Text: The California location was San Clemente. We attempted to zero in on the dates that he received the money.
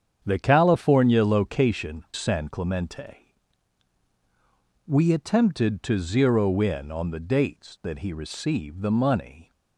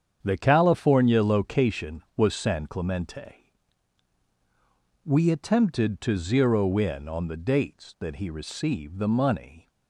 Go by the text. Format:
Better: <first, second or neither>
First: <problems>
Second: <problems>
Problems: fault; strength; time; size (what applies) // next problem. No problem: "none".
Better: second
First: starts louder than the rest; strong; until 1.2 s; 8 dB // skips "was"; at 2.1 s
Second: starts louder than the rest; strong; until 1.2 s; 8 dB